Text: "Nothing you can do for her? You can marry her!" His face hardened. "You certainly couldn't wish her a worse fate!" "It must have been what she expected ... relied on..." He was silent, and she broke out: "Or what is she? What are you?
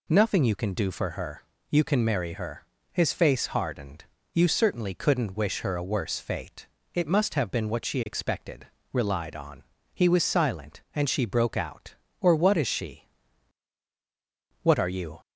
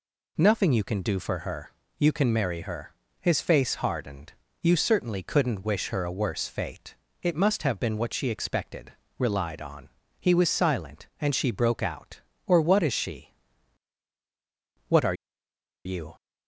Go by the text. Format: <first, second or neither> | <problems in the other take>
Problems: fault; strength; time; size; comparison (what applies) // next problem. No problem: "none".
first | pauses between "are" and "you"; noticeable; at 15.1 s; 0.70 s long